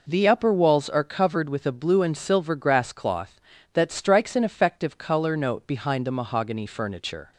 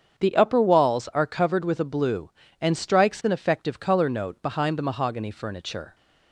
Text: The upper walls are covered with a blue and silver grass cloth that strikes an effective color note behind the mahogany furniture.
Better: first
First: none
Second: starts louder than the rest; strong; until 1.1 s; 7.5 dB // skips "silver grass cloth that"; at 2.7 s

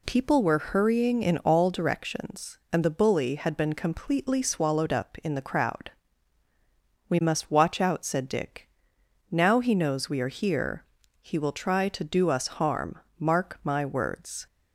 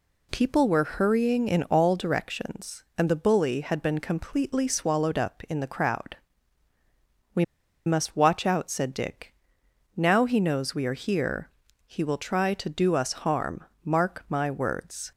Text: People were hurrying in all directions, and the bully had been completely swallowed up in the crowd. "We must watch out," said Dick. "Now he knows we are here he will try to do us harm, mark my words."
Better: first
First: pauses between "here" and "he"; slight; at 10.8 s; 0.36 s long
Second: pauses between "We" and "must"; at 7.4 s; 0.42 s long // pauses between "here" and "he"; slight; at 11.4 s; 0.36 s long

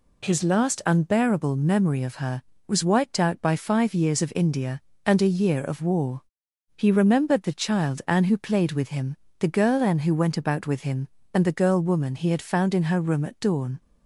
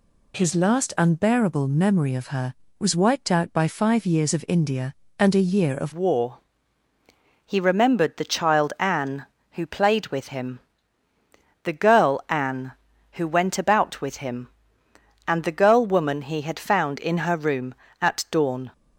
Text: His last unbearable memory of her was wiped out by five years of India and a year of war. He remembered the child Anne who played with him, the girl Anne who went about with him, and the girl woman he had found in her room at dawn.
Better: first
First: none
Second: changes voice at "war"; from 5.9 s on; 12.8 s long

